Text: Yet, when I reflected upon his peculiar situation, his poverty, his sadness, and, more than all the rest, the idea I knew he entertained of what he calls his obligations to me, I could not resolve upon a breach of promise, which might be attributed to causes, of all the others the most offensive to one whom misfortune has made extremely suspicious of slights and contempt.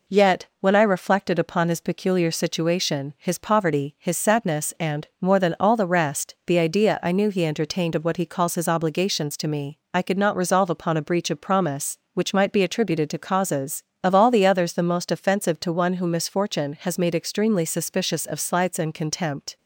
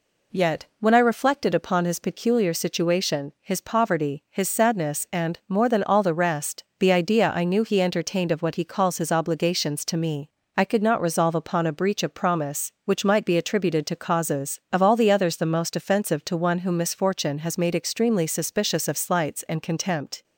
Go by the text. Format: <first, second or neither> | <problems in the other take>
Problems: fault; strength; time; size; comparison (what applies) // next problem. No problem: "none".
neither | none